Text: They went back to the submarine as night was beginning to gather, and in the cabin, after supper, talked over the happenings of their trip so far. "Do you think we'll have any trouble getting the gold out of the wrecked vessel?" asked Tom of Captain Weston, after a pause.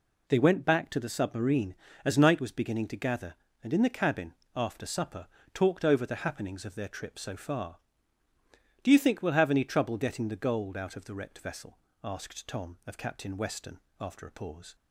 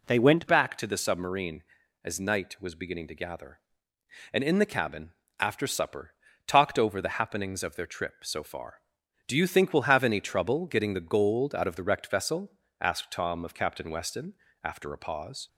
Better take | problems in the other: first | changes voice at "back"; from 0.4 s on; 15.0 s long

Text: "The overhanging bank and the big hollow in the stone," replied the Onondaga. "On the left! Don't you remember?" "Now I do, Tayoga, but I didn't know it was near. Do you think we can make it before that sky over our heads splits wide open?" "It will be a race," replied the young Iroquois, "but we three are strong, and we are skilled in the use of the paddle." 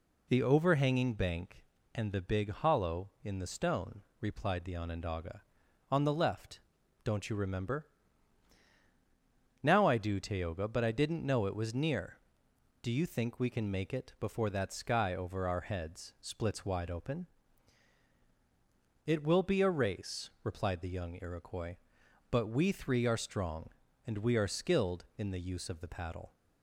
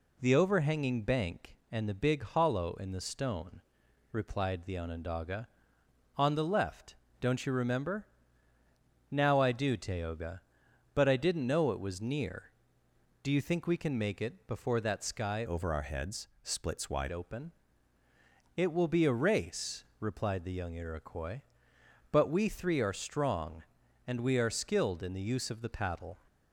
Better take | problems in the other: first | changes voice from "over" to "wide"; from 15.4 to 17.1 s; 1.7 s long

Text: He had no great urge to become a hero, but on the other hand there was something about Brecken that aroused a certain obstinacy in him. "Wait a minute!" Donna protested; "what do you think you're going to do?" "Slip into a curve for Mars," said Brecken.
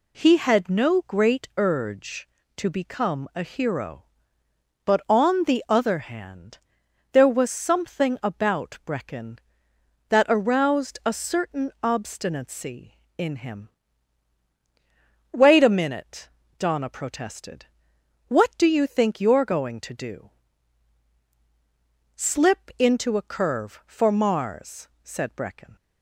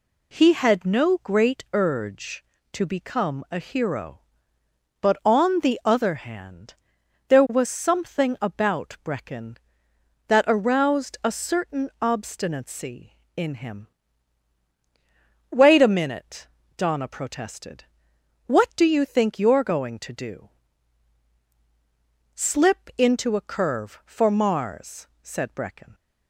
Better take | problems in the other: neither | pauses between "hand" and "there"; noticeable; the same in both

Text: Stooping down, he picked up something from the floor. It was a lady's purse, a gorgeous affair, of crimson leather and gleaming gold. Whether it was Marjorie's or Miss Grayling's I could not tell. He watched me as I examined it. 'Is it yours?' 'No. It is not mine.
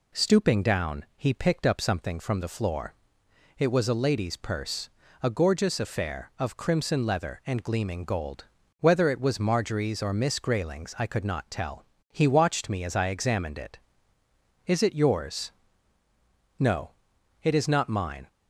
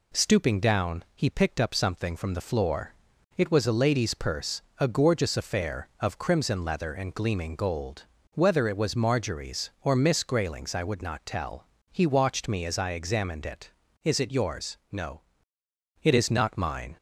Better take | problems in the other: first | says "would" for "could"; at 10.8 s

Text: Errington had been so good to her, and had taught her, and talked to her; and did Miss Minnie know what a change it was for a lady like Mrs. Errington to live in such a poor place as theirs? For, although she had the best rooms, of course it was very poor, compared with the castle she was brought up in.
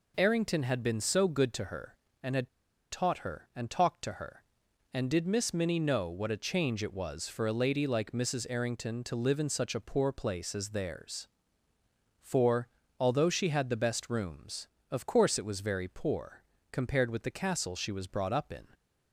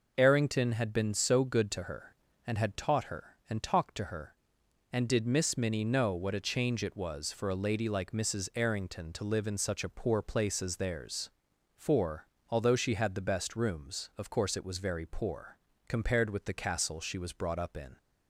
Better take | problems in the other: second | pauses between "had" and "taught"; at 2.4 s; 0.41 s long

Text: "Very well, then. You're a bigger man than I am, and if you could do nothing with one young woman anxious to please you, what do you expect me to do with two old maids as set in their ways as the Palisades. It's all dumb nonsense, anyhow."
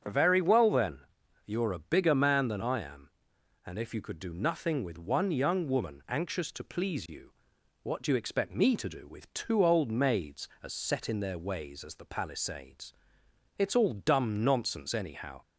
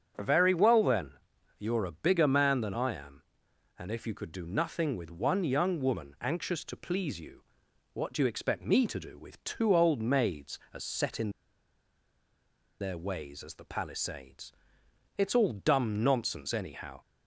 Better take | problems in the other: first | starts louder than the rest; strong; until 1.6 s; 7.5 dB; strong in the first // pauses between "in" and "their"; strong; at 11.3 s; 1.4 s long

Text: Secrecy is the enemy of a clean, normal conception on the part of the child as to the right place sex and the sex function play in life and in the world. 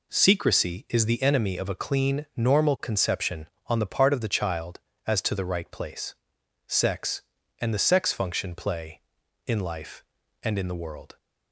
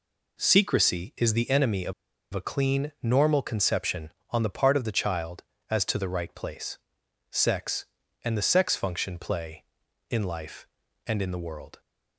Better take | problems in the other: first | pauses between "of" and "a"; at 1.9 s; 0.42 s long // pauses between "place" and "sex"; noticeable; at 6.7 s; 0.54 s long; noticeable in the first

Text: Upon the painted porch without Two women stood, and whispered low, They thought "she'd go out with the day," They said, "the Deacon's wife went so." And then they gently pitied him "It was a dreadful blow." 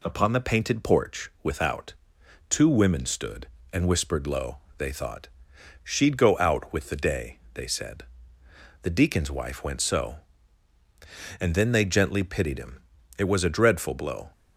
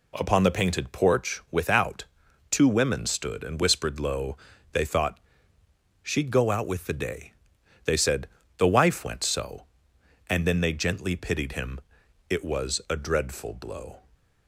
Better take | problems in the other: first | pauses between "without" and "Two"; noticeable; at 2.0 s; 0.48 s long; noticeable in the first // pauses between "thought" and "she'd"; noticeable; at 5.1 s; 0.86 s long; noticeable in the first // skips "Deacon's"; at 8.6 s // pauses between "him" and "It"; noticeable; at 11.7 s; 0.50 s long; also in the first

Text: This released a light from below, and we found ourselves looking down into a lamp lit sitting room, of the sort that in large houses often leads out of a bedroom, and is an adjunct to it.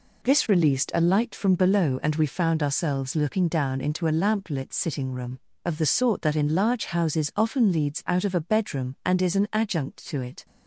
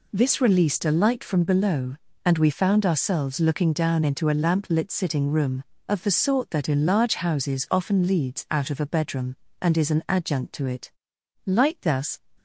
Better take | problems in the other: first | goes on to say "Light thus"; noticeable; from 11.4 s on; 0.74 s long

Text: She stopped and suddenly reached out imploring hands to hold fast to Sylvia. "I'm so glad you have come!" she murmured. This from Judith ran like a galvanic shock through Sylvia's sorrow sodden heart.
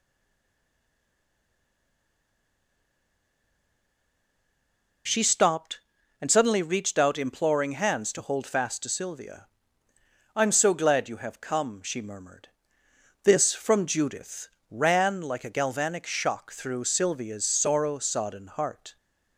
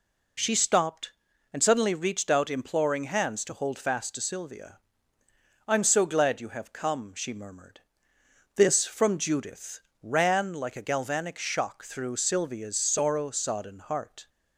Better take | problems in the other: second | stays silent before the first word; strong; until 5.0 s; 5.0 s long // pauses between "Judith" and "ran"; slight; at 14.4 s; 0.20 s long; slight in the second

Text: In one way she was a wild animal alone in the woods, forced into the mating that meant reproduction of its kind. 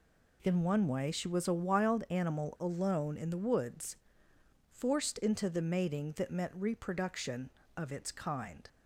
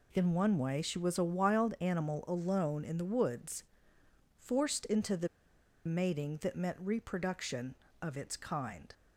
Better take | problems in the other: first | pauses between "the" and "mating"; noticeable; at 5.2 s; 0.59 s long

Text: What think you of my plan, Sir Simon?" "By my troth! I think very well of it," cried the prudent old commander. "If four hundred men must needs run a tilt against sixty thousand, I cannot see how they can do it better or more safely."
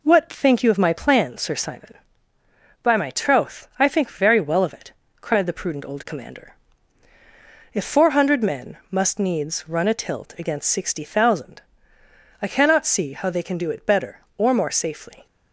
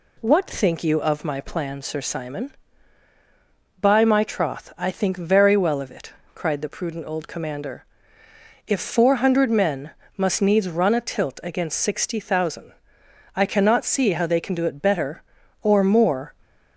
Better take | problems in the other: first | pauses between "men" and "must"; slight; at 9.9 s; 0.24 s long // stops before "safely"; at 16.4 s

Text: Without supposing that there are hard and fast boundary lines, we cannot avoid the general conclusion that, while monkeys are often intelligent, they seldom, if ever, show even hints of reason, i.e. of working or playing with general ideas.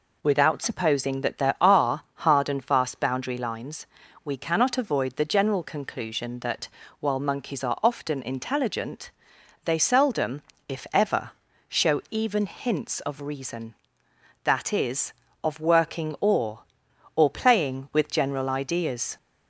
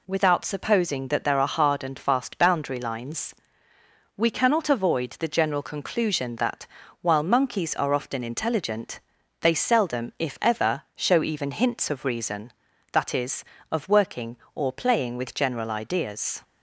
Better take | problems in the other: second | says "or" twice; at 17.1 s

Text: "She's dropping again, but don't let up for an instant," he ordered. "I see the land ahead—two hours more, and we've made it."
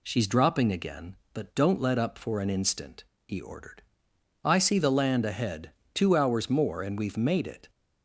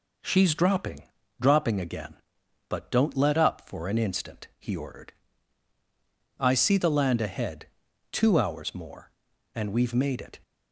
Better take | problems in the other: first | says "dropping" twice; at 1.4 s

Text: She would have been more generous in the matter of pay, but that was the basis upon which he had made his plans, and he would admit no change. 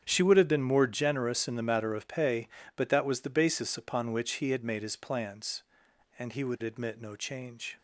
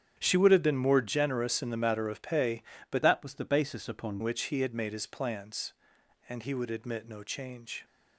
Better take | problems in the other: first | starts louder than the rest; strong; until 1.1 s; 9 dB; strong in the first // changes voice from "that" to "upon"; from 3.0 to 4.2 s; 1.2 s long

